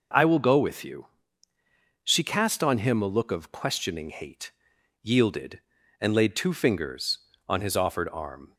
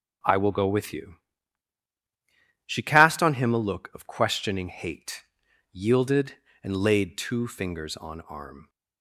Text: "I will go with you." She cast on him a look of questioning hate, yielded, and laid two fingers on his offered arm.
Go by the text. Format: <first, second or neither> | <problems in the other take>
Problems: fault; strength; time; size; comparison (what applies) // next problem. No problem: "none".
first | skips "his offered"; at 8.2 s